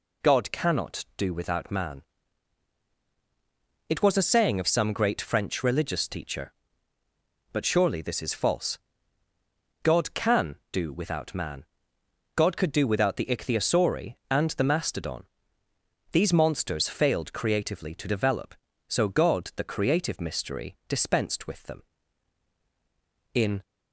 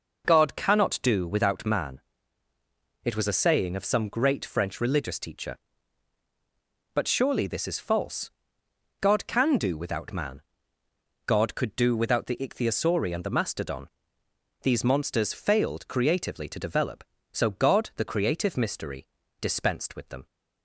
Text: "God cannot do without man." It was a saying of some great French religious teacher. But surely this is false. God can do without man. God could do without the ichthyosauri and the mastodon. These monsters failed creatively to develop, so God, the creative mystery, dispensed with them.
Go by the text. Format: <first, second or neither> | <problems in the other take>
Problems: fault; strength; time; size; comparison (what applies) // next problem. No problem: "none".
second | goes on to say "In"; slight; from 23.3 s on; 0.30 s long